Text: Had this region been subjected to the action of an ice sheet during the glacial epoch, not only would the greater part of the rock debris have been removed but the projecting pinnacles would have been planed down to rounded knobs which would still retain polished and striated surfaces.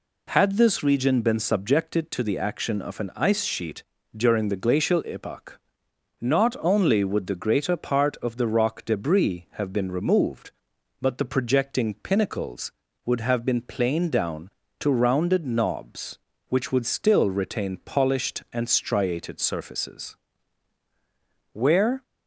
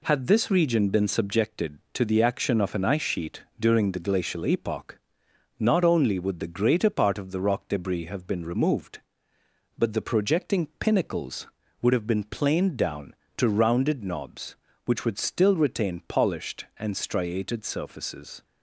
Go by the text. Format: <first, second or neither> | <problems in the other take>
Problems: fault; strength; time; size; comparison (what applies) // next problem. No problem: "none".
second | pauses between "sheet" and "during"; slight; at 3.8 s; 0.32 s long // goes on to say "Where"; from 21.5 s on; 0.50 s long